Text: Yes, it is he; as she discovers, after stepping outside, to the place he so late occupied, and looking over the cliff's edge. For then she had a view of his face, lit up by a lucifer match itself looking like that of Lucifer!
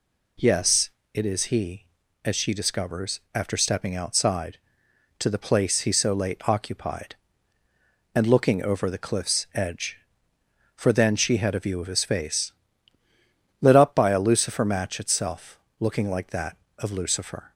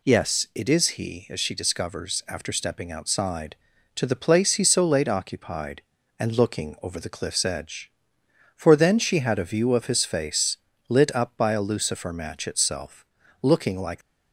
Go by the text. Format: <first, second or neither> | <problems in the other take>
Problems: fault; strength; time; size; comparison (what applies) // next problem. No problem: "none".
first | pauses between "itself" and "looking"; at 13.0 s; 0.40 s long; slight in the first // stops before "that of Lucifer"; at 14.0 s